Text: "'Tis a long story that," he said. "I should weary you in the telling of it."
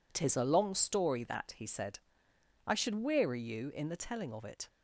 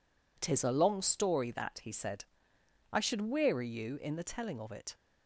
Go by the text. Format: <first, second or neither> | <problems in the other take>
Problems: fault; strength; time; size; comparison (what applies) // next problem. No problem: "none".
neither | none